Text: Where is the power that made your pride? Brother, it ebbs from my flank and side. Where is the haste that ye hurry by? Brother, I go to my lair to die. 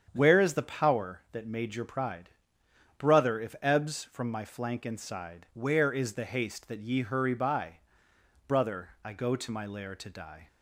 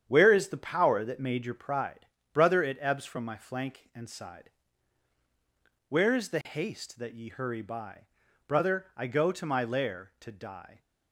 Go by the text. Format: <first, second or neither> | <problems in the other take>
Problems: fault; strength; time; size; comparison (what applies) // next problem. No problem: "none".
second | starts louder than the rest; strong; until 1.1 s; 8 dB; strong in the second // says "if" for "it"; at 3.3 s